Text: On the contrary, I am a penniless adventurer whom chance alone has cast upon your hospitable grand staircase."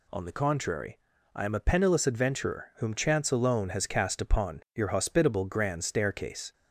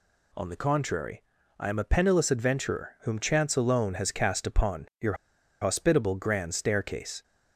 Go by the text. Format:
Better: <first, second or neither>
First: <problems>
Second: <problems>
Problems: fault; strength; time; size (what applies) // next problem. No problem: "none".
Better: first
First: none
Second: pauses between "your" and "hospitable"; noticeable; at 5.1 s; 0.47 s long